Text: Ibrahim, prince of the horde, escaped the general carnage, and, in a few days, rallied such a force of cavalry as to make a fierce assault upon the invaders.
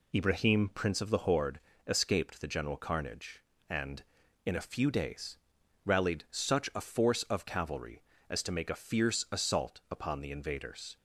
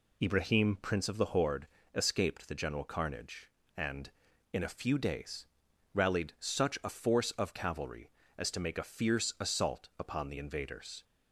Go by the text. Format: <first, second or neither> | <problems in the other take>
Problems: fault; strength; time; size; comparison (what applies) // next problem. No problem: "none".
neither | none